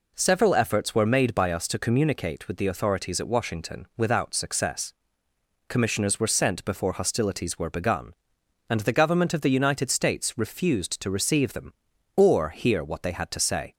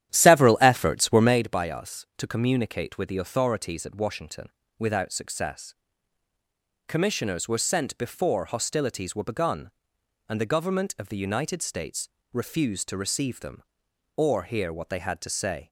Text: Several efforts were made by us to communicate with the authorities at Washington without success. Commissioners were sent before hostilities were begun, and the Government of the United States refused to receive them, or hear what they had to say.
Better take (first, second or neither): first